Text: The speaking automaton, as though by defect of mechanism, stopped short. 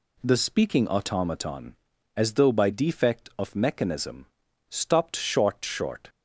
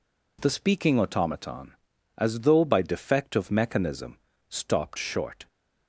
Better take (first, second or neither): second